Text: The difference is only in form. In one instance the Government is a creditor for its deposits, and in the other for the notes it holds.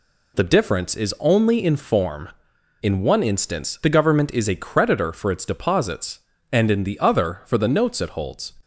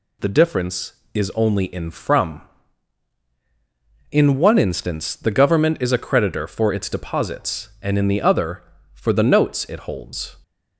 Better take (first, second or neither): first